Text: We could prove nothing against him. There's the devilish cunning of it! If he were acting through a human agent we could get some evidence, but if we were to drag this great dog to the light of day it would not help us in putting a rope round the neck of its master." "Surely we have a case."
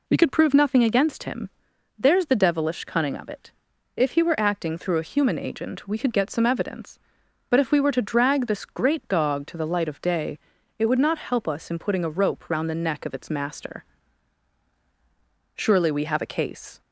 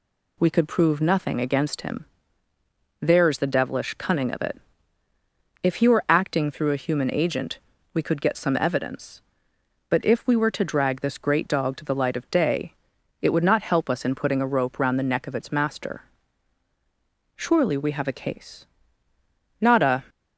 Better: first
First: pauses between "day" and "it"; at 10.3 s; 0.40 s long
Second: pauses between "agent" and "we"; slight; at 7.5 s; 0.34 s long // pauses between "day" and "it"; noticeable; at 12.7 s; 0.48 s long // goes on to say "Not a"; slight; from 19.5 s on; 0.46 s long

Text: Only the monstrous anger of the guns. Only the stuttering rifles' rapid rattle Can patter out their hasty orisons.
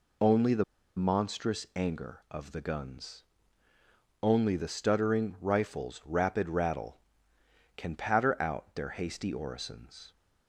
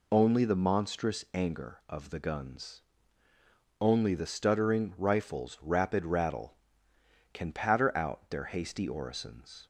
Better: second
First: pauses between "the" and "monstrous"; slight; at 0.6 s; 0.32 s long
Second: none

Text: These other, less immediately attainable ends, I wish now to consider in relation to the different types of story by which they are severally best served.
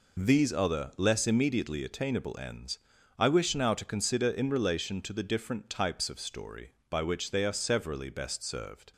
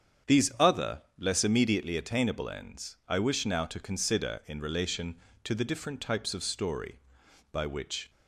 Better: first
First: none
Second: starts louder than the rest; strong; until 1.4 s; 8 dB // stops before "they are severally best served"; at 8.0 s

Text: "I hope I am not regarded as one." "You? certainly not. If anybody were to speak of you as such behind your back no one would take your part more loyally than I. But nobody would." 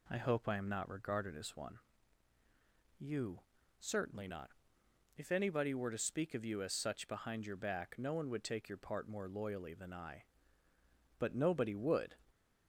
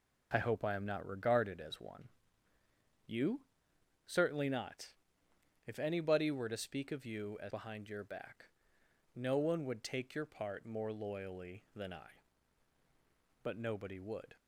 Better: first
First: none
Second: skips "such"; at 7.5 s // pauses between "back" and "no"; noticeable; at 8.4 s; 0.66 s long

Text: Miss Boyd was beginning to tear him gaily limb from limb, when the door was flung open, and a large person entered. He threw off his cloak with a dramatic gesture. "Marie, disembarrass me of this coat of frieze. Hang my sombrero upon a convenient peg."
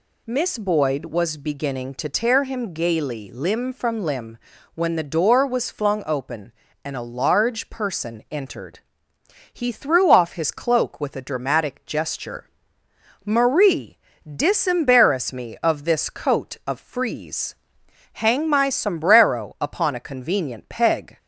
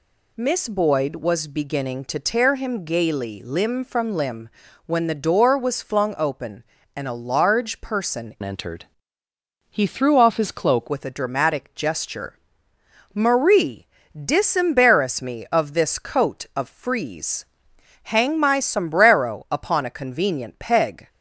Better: first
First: none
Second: changes voice from "entered" to "cloak"; from 8.4 to 10.8 s; 2.4 s long

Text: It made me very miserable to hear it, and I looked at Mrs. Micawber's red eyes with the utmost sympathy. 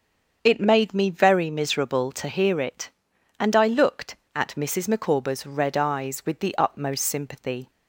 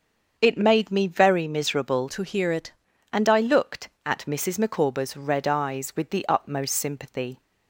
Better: first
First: starts louder than the rest; until 1.4 s; 7 dB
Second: starts louder than the rest; until 1.3 s; 7 dB // changes voice from "to" to "it"; from 2.0 to 2.7 s; 0.7 s long

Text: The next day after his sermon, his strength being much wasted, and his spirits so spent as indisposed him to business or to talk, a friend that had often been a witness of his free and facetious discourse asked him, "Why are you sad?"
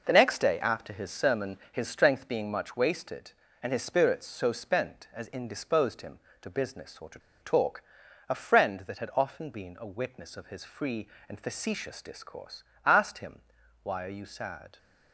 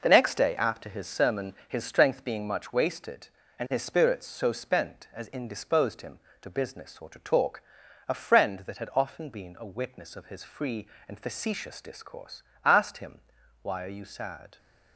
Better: second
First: pauses between "to" and "talk"; slight; at 7.1 s; 0.22 s long // pauses between "discourse" and "asked"; slight; at 12.6 s; 0.20 s long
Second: pauses between "discourse" and "asked"; slight; at 12.4 s; 0.20 s long

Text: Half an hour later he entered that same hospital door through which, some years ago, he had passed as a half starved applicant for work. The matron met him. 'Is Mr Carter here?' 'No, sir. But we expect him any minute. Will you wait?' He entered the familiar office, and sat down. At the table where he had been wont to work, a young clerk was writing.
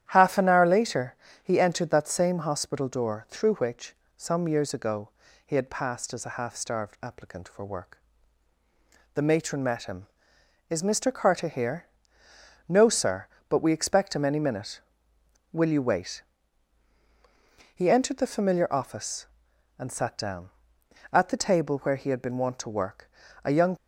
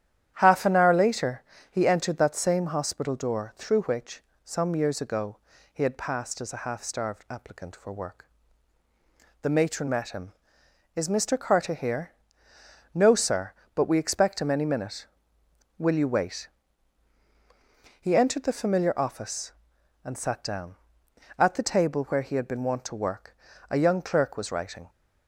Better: second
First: starts louder than the rest; strong; until 1.1 s; 10.5 dB // pauses between "later" and "he"; slight; at 1.1 s; 0.28 s long // stops before "clerk was writing"; at 23.7 s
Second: starts louder than the rest; strong; until 1.3 s; 10.5 dB // pauses between "later" and "he"; slight; at 1.4 s; 0.28 s long

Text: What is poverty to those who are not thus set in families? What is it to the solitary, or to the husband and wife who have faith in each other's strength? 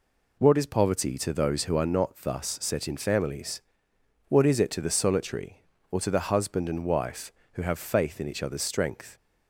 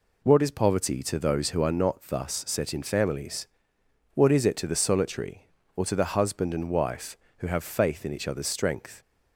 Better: neither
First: none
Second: none

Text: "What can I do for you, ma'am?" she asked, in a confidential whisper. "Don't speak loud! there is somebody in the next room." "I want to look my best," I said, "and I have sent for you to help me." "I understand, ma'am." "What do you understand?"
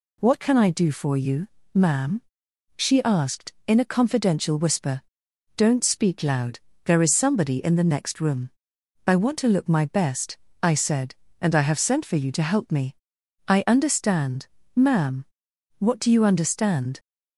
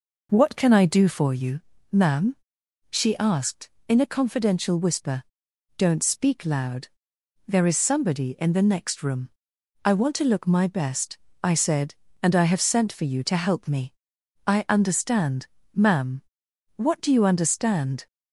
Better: first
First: none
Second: starts louder than the rest; noticeable; until 1.4 s; 5 dB

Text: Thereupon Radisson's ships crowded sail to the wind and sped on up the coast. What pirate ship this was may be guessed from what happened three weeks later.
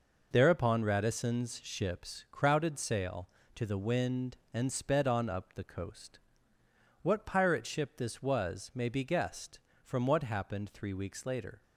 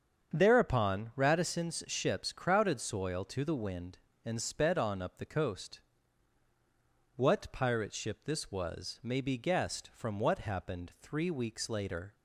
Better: first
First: none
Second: starts louder than the rest; strong; until 1.3 s; 7.5 dB // says "soil" for "sail"; at 2.8 s

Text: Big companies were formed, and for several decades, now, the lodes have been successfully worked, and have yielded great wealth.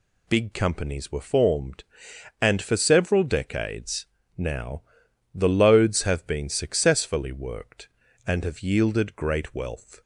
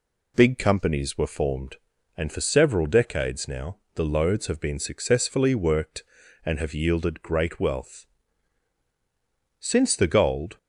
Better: first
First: none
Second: goes on to say "Since the gold"; noticeable; from 9.5 s on; 0.98 s long

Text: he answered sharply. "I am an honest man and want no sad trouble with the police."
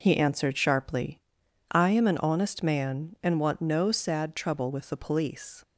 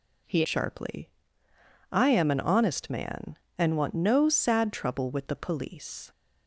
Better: first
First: none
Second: skips "answered"; at 0.4 s

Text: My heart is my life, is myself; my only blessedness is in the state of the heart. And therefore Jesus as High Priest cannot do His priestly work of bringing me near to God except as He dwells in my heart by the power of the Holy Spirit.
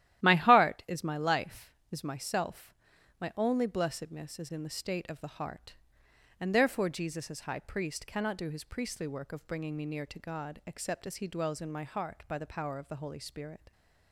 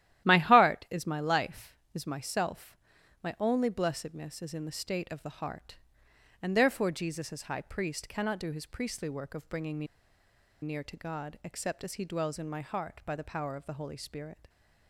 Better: first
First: starts louder than the rest; strong; until 1.2 s; 12.5 dB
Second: starts louder than the rest; strong; until 1.3 s; 12.5 dB // pauses between "me" and "near"; noticeable; at 9.8 s; 0.76 s long

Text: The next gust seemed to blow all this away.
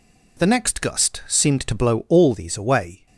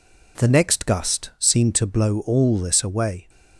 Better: second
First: says "these" for "this"; at 2.3 s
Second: none

